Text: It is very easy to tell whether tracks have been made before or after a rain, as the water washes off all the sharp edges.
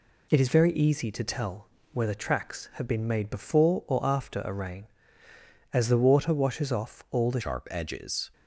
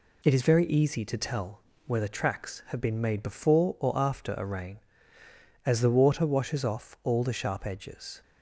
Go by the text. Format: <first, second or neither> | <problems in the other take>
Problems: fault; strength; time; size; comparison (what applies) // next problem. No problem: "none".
second | pauses between "tell" and "whether"; slight; at 1.6 s; 0.26 s long; slight in the second // changes voice at "sharp"; from 7.4 s on; 0.9 s long